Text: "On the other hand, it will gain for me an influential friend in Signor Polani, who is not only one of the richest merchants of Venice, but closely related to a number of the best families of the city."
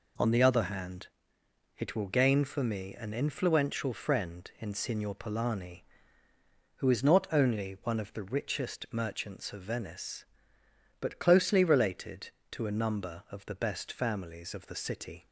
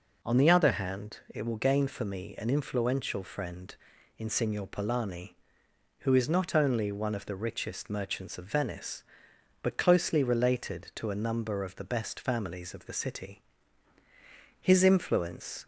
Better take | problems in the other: first | goes on to say "His influence"; noticeable; from 14.5 s on; 1.0 s long

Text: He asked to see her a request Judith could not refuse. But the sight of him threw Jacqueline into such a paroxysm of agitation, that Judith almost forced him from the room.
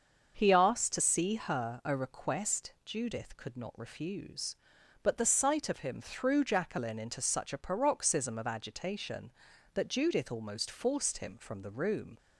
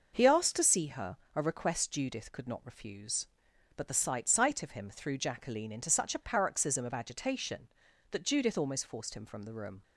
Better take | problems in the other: first | starts louder than the rest; until 1.4 s; 6 dB; also in the first // pauses between "her" and "a"; slight; at 1.1 s; 0.18 s long // says "sight" twice; at 4.2 s

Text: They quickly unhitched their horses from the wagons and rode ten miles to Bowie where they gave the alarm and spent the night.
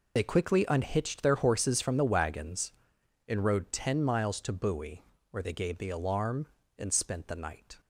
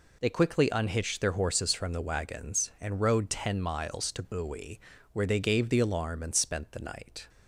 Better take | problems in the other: second | loses the start of "They"; at 0.1 s; 35 ms // pauses between "Bowie" and "where"; slight; at 5.0 s; 0.28 s long; slight in the second

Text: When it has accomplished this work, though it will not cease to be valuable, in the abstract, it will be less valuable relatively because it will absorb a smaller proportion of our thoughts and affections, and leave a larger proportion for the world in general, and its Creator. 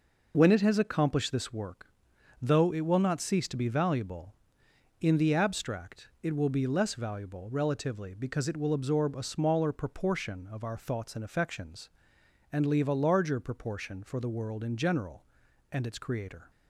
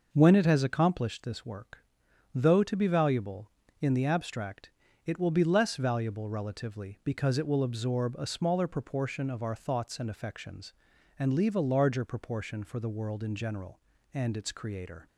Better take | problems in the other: first | skips "it will not cease"; at 2.6 s

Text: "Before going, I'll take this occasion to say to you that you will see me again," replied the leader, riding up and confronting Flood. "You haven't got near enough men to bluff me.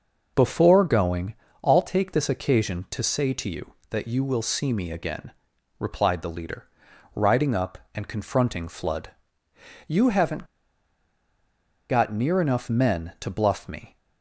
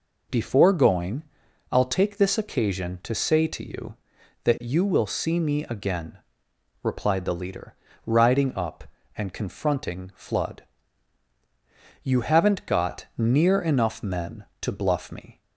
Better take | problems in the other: second | pauses between "haven't" and "got"; strong; at 10.4 s; 1.4 s long

